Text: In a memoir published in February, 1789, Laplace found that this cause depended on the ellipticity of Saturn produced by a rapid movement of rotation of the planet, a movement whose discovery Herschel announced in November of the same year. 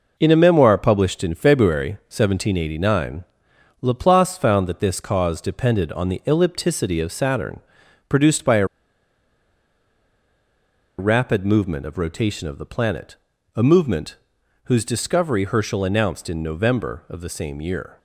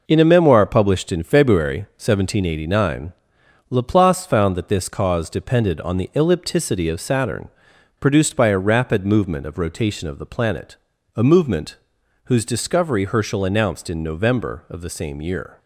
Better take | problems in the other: second | pauses between "Saturn" and "produced"; noticeable; at 7.6 s; 0.48 s long; noticeable in the second // pauses between "a" and "rapid"; strong; at 8.6 s; 2.3 s long // pauses between "movement" and "whose"; noticeable; at 14.1 s; 0.48 s long; noticeable in the second

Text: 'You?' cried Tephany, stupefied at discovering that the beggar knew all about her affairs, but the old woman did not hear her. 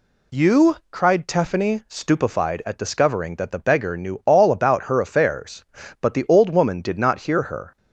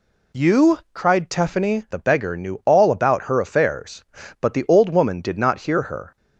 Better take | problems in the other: first | skips "stupefied at discovering that"; at 1.8 s

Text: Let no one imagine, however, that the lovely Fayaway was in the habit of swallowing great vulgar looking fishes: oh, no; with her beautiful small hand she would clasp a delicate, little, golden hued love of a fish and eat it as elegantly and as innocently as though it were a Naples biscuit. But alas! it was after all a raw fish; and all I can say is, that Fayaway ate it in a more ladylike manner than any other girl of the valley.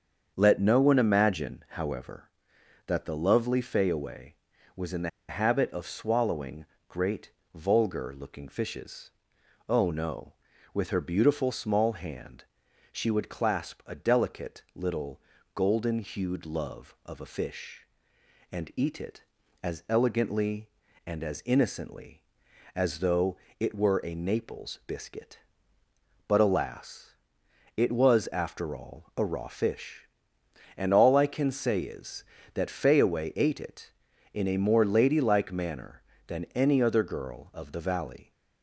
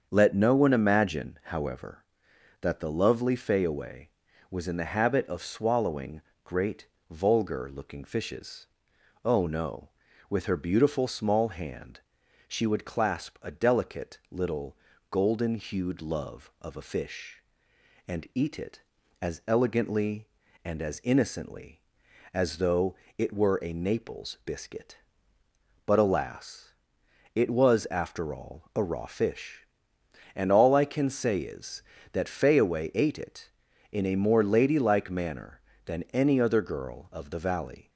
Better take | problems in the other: second | starts louder than the rest; until 1.3 s; 7 dB; also in the second // pauses between "the" and "habit"; slight; at 5.0 s; 0.18 s long // pauses between "swallowing" and "great"; slight; at 6.6 s; 0.24 s long; slight in the second // pauses between "great" and "vulgar"; slight; at 7.3 s; 0.24 s long; slight in the second // pauses between "hand" and "she"; noticeable; at 12.4 s; 0.48 s long; noticeable in the second // pauses between "though" and "it"; slight; at 23.3 s; 0.24 s long; slight in the second

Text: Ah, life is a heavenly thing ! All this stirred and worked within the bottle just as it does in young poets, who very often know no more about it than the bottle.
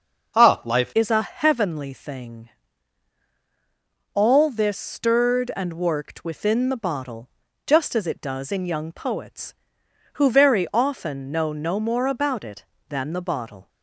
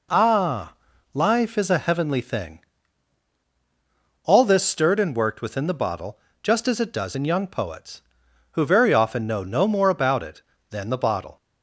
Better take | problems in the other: second | changes voice at "is"; from 0.9 s on; 12.7 s long // pauses between "bottle" and "just"; at 7.2 s; 0.38 s long; slight in the second

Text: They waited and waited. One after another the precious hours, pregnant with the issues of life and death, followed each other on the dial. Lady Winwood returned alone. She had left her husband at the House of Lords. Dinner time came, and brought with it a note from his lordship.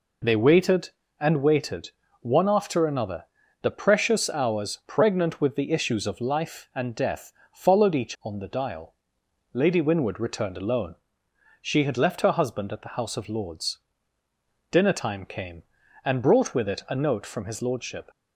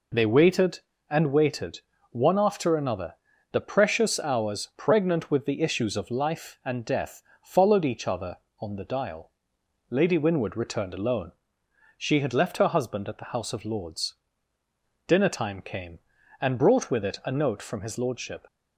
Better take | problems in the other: second | pauses between "another" and "the"; slight; at 3.2 s; 0.36 s long; slight in the second // skips "other"; at 8.1 s

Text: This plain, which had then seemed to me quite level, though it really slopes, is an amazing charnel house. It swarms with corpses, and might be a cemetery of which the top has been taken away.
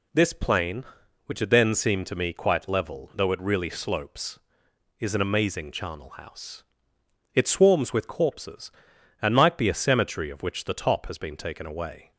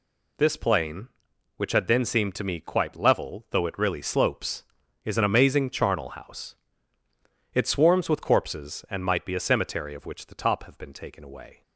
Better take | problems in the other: first | says "have" for "has"; at 10.6 s

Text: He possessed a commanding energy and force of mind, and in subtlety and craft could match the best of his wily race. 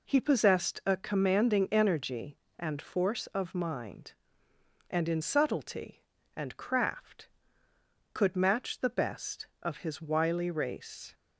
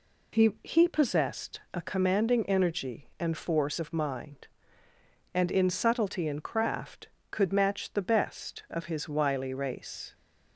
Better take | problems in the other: first | says "He" twice; at 0.6 s

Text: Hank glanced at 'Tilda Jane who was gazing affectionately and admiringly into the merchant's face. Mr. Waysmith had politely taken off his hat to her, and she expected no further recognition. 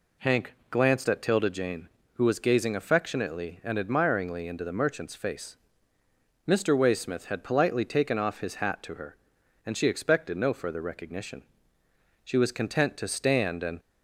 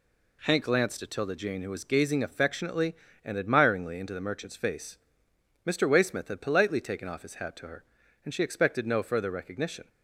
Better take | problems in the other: second | goes on to say "She was content to stand and"; from 12.2 s on; 1.5 s long

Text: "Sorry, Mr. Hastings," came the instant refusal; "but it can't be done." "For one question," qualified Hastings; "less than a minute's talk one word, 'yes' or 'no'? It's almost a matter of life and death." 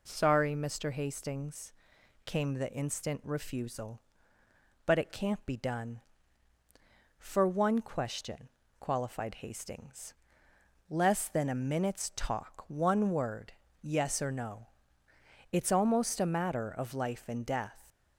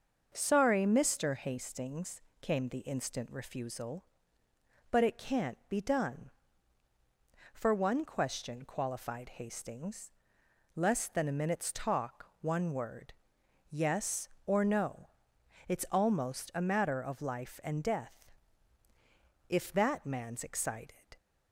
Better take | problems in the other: first | starts louder than the rest; until 1.3 s; 6.5 dB // goes on to say "If that man's excited"; from 19.4 s on; 1.4 s long

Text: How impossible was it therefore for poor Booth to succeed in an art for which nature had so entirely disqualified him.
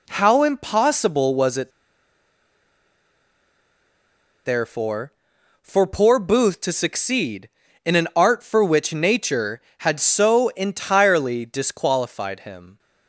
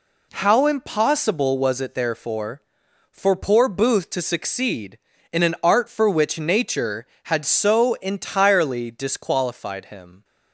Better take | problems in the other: second | pauses between "it" and "therefore"; strong; at 1.7 s; 2.7 s long

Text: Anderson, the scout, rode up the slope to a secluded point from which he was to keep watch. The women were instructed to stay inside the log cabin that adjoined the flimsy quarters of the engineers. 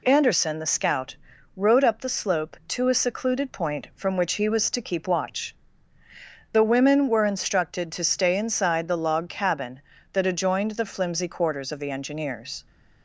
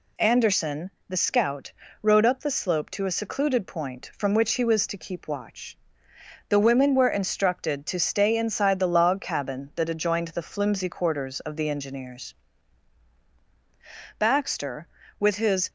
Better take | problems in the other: first | goes on to say "Baxter with his"; from 14.1 s on; 1.5 s long

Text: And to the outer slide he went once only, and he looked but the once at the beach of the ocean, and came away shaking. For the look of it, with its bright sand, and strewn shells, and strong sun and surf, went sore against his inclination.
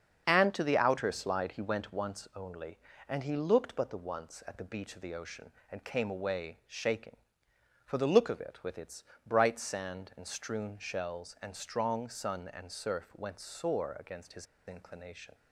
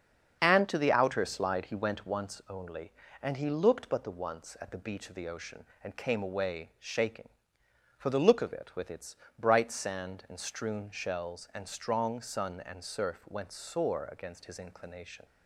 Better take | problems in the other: second | starts louder than the rest; until 1.2 s; 7 dB; also in the second // pauses between "its" and "bright"; slight; at 9.0 s; 0.24 s long; slight in the second // pauses between "his" and "inclination"; slight; at 14.4 s; 0.22 s long

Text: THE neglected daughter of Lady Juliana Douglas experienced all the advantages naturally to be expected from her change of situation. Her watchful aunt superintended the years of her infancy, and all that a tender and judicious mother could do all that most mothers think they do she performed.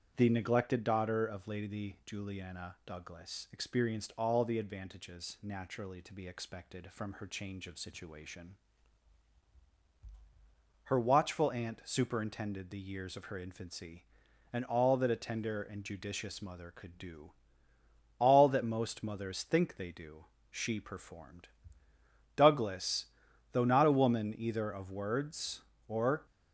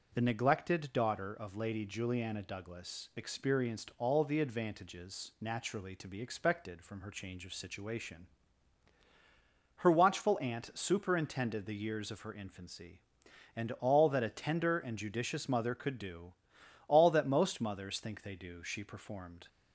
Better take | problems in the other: second | starts louder than the rest; strong; until 1.1 s; 8.5 dB // pauses between "do" and "all"; noticeable; at 17.3 s; 0.86 s long; noticeable in the second // pauses between "do" and "she"; slight; at 20.2 s; 0.26 s long // goes on to say "Douglas though not a woman either of words or"; strong; from 22.3 s on; 3.9 s long

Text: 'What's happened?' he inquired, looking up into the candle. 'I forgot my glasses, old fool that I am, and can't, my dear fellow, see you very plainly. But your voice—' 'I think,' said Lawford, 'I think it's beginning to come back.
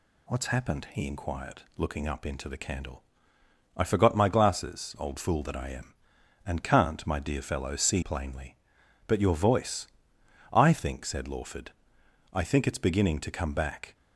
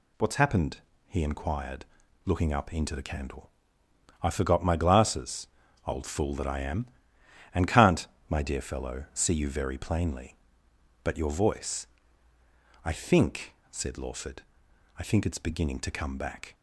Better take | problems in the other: second | skips "you very"; at 8.0 s

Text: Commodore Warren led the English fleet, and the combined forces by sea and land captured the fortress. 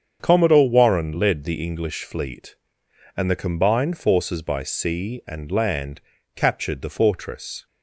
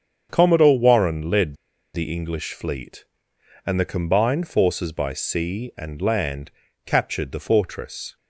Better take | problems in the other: first | starts louder than the rest; strong; until 1.3 s; 7.5 dB; strong in the first // pauses between "led" and "the"; at 1.5 s; 0.38 s long // pauses between "land" and "captured"; slight; at 6.5 s; 0.34 s long; slight in the first

